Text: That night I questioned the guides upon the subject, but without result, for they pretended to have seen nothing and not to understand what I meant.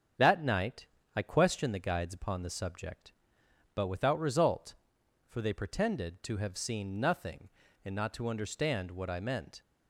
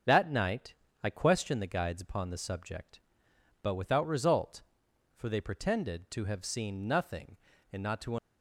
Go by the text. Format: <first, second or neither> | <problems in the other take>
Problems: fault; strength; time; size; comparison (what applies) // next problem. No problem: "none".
first | starts louder than the rest; until 1.3 s; 7 dB; strong in the first // pauses between "night" and "I"; slight; at 0.7 s; 0.28 s long; slight in the first // stops before "understand what I meant"; at 8.1 s